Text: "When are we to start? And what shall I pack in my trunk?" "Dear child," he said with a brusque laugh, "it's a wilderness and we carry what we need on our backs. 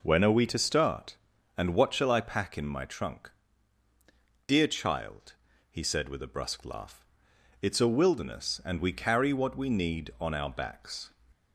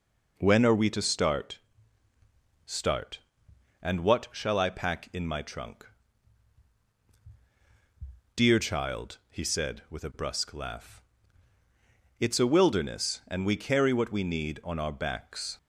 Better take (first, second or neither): first